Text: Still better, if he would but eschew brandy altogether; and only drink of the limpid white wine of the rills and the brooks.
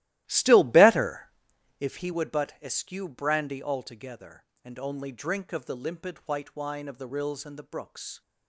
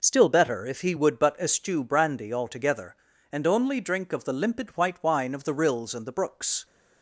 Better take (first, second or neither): second